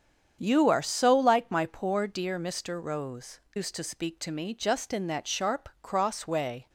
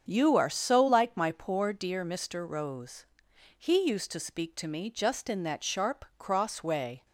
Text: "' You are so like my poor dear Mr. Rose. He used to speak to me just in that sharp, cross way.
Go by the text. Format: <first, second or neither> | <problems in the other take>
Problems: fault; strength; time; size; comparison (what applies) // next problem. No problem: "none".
second | starts louder than the rest; strong; until 1.4 s; 8 dB; strong in the second // skips "He"; at 3.4 s